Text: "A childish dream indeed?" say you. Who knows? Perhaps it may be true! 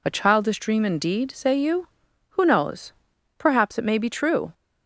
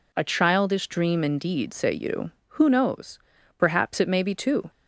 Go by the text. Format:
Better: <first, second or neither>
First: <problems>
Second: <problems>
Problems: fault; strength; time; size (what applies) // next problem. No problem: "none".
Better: first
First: none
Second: says "two" for "true"; at 4.3 s